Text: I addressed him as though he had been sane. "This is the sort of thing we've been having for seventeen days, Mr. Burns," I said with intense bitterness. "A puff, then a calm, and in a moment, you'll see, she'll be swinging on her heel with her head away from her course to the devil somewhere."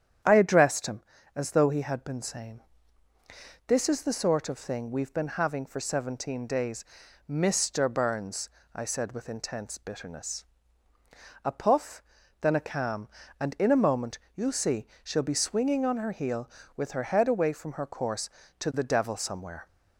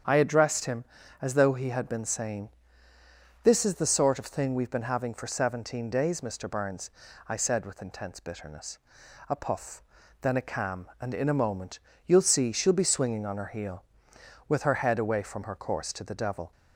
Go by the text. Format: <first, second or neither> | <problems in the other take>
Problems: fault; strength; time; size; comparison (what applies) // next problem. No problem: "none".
first | starts louder than the rest; strong; until 1.4 s; 8 dB; strong in the first // stops before "somewhere"; at 16.5 s